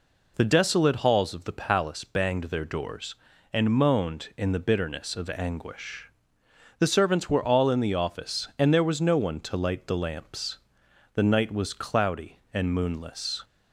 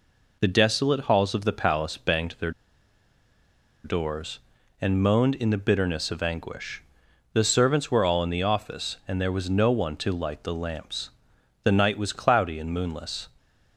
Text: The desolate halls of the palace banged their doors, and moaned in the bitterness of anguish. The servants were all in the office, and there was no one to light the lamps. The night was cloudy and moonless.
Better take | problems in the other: first | pauses between "their" and "doors"; strong; at 2.5 s; 1.3 s long

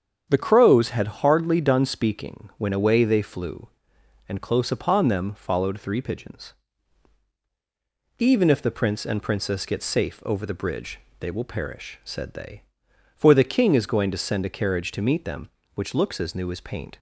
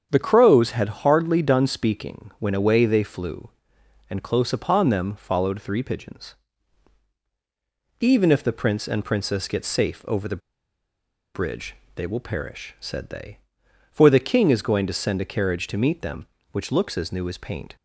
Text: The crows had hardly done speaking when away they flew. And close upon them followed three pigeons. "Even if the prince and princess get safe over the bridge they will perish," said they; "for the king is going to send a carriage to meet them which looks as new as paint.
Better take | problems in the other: first | starts louder than the rest; strong; until 1.1 s; 7.5 dB; strong in the first // pauses between "the" and "bridge"; noticeable; at 10.4 s; 0.94 s long // pauses between "bridge" and "they"; slight; at 11.7 s; 0.20 s long; slight in the first

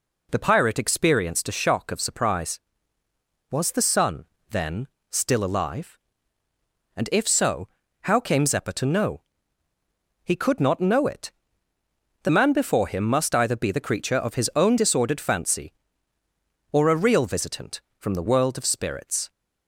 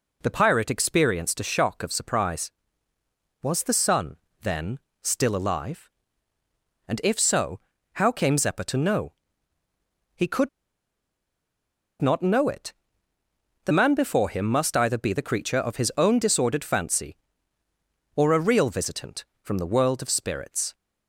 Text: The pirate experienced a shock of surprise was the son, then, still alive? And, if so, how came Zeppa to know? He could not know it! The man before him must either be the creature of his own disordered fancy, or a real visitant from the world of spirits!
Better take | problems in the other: first | pauses between "could" and "not"; strong; at 10.4 s; 1.5 s long

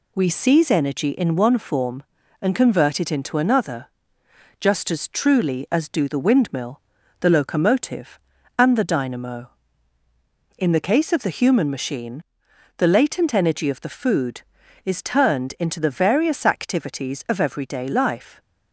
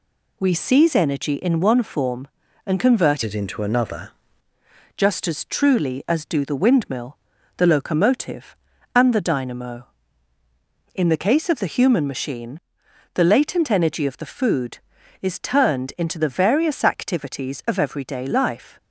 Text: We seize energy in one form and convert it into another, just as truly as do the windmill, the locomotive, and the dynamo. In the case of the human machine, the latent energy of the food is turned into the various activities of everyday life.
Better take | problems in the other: first | changes voice from "it" to "another"; from 3.2 to 4.0 s; 0.8 s long

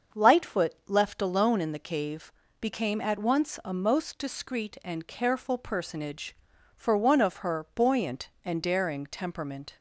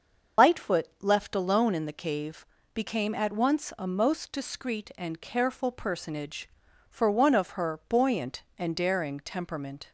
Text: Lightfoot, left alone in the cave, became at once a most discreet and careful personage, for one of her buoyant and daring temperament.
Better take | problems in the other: first | loses the start of "Lightfoot"; at 0.3 s; 120 ms // starts louder than the rest; until 1.5 s; 6.5 dB; also in the first

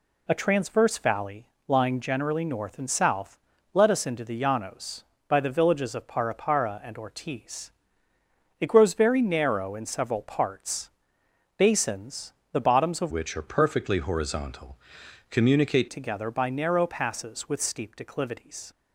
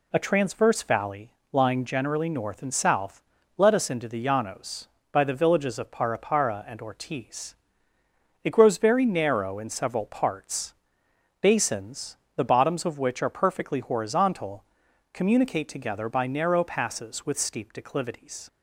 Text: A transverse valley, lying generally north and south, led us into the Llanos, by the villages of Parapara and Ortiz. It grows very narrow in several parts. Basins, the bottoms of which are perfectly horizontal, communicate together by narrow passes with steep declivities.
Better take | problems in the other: second | changes voice from "which" to "communicate"; from 13.1 to 15.8 s; 2.7 s long

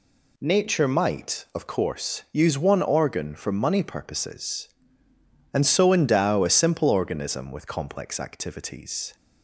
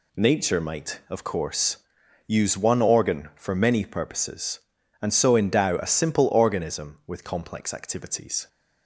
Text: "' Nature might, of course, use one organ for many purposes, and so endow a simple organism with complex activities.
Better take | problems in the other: second | says "money" for "many"; at 3.5 s

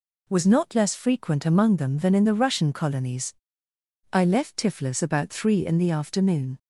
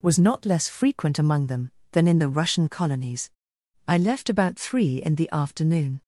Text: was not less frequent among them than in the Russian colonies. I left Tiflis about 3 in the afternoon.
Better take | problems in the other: first | skips "Tiflis"; at 4.2 s

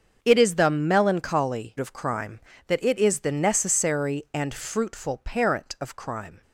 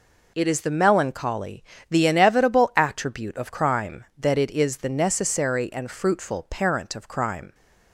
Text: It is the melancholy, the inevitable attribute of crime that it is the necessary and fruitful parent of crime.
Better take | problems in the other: second | starts louder than the rest; until 1.2 s; 6.5 dB // skips "the inevitable attribute"; at 1.7 s

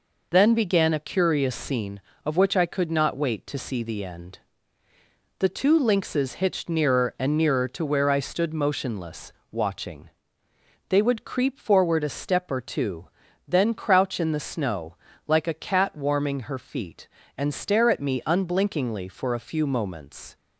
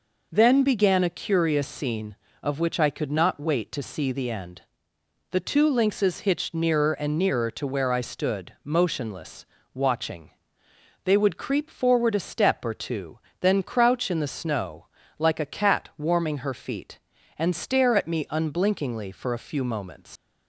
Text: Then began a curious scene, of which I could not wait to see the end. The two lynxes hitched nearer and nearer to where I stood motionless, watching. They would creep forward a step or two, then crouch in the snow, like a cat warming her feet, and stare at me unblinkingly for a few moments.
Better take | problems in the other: first | leaves "moments" unfinished; at 20.1 s; 90 ms

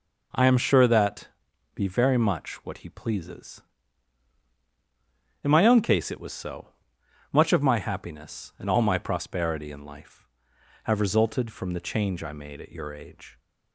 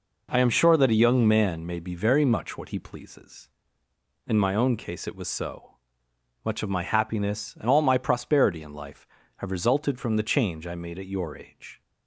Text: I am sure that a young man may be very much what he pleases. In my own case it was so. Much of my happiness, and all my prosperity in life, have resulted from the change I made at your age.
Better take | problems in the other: second | skips "a young man may"; at 1.5 s

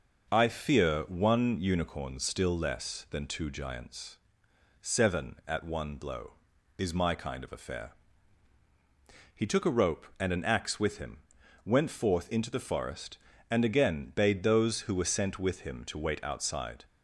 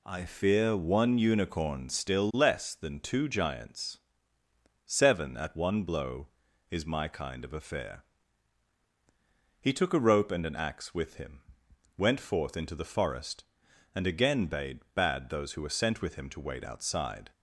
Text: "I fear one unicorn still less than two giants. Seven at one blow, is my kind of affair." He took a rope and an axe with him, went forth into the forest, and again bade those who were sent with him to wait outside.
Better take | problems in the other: first | says "bade" twice; at 14.9 s

